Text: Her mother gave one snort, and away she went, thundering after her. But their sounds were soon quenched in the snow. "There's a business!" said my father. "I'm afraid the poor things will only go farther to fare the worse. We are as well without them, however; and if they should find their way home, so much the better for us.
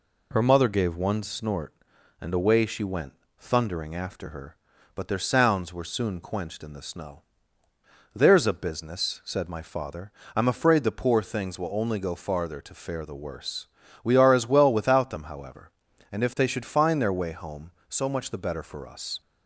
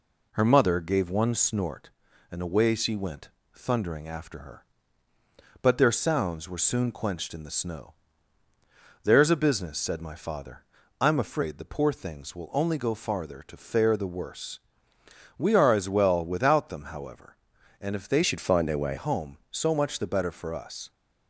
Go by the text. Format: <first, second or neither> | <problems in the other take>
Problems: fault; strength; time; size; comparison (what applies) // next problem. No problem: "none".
first | changes voice from "should" to "way"; from 18.2 to 18.9 s; 0.7 s long